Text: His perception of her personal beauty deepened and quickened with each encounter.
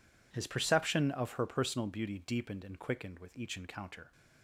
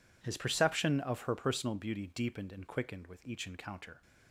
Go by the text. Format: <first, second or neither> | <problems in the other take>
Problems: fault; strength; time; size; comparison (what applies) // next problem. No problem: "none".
neither | none